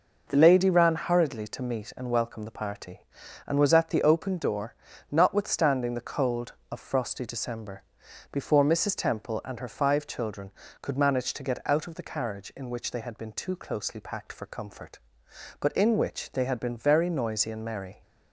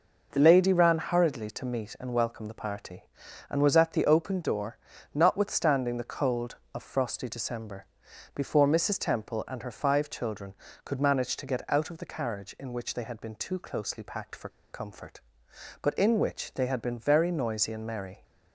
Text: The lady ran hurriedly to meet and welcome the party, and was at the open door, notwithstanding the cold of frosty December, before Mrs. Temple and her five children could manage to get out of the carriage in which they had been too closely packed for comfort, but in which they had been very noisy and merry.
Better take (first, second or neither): first